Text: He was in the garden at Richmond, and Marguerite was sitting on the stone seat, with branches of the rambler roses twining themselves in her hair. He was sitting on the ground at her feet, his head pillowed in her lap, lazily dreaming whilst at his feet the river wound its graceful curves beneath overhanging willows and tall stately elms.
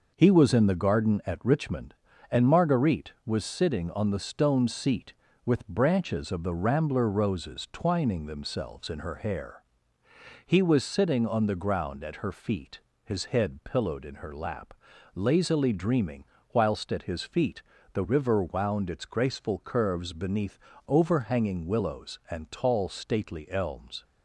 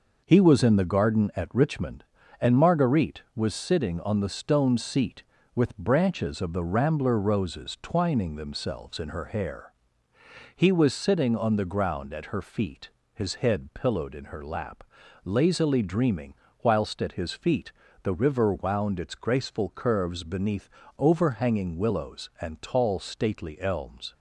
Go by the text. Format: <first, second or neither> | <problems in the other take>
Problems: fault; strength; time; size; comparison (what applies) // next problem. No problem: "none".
neither | pauses between "dreaming" and "whilst"; slight; the same in both // pauses between "feet" and "the"; slight; the same in both // pauses between "beneath" and "overhanging"; slight; the same in both